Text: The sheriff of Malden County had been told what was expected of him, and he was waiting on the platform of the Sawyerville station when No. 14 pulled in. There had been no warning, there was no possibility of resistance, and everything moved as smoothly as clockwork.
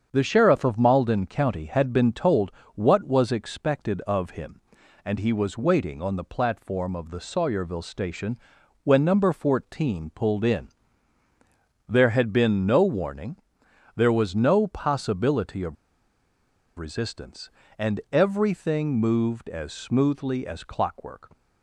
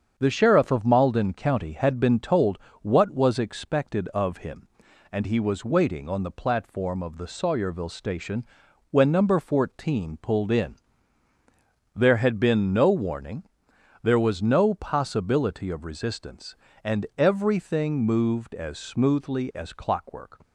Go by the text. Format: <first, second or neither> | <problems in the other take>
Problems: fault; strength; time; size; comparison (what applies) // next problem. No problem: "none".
second | starts louder than the rest; strong; until 1.1 s; 7.5 dB; strong in the second // pauses between "told" and "what"; slight; at 2.4 s; 0.24 s long; slight in the second // pauses between "station" and "when"; noticeable; at 8.3 s; 0.46 s long; noticeable in the second // pauses between "of" and "resistance"; at 15.7 s; 1.0 s long